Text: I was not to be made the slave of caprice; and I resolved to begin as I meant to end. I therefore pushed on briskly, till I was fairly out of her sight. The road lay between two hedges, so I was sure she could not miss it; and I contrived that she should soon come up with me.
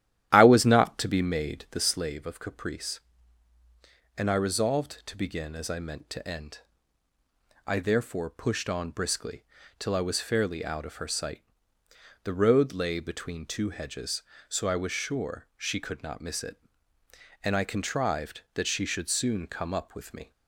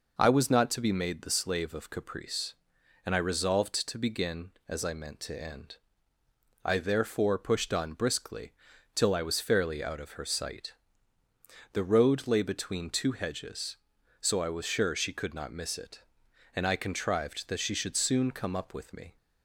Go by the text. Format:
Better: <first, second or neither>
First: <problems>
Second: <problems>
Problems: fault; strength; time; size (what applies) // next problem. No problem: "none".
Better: second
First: starts louder than the rest; strong; until 1.8 s; 12 dB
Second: none